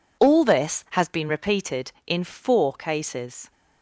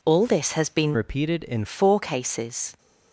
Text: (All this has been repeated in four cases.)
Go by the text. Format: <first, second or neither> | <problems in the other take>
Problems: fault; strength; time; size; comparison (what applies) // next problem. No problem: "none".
first | changes voice from "repeated" to "in"; from 0.9 to 1.6 s; 0.7 s long